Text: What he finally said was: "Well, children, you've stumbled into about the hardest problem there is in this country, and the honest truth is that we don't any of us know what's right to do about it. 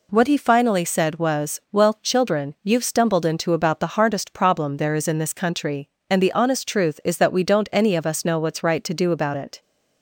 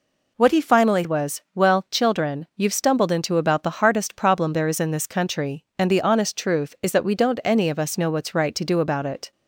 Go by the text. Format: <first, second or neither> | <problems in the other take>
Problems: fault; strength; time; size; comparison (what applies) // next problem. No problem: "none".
first | skips "said"; at 1.0 s